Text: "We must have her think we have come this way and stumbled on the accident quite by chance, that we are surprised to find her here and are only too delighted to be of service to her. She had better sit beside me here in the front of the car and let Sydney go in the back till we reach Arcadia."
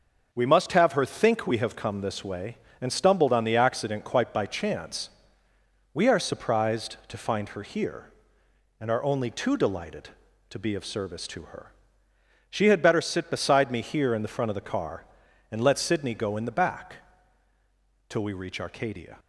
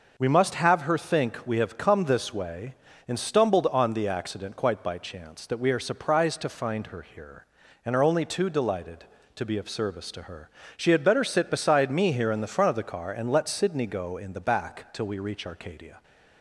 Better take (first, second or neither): second